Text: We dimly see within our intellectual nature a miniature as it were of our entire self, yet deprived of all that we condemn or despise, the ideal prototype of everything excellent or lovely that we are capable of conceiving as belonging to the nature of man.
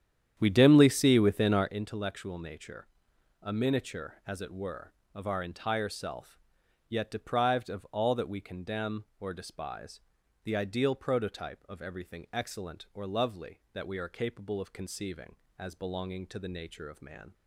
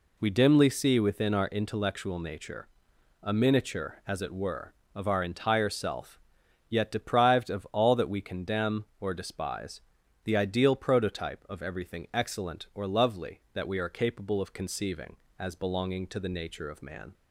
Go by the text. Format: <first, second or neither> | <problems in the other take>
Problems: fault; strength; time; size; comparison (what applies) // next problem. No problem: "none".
second | starts louder than the rest; strong; until 1.8 s; 9.5 dB // pauses between "nature" and "a"; noticeable; at 2.8 s; 0.54 s long; noticeable in the second